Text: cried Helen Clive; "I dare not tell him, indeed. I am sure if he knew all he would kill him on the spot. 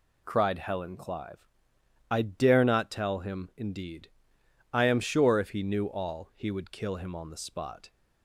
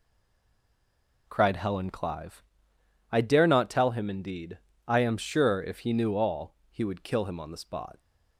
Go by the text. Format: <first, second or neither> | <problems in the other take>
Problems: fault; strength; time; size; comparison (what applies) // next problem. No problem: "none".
first | stays silent before the first word; noticeable; until 1.2 s; 1.2 s long // pauses between "all" and "he"; slight; at 6.5 s; 0.16 s long